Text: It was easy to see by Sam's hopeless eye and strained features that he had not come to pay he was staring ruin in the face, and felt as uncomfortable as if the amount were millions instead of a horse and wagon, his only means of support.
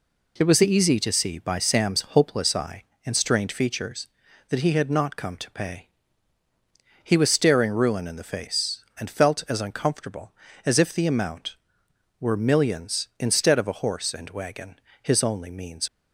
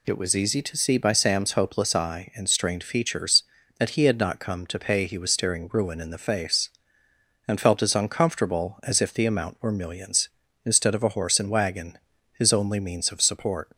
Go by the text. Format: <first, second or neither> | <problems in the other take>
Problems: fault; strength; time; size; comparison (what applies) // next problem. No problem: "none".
second | pauses between "pay" and "he"; at 5.8 s; 1.1 s long // stops before "of support"; at 15.8 s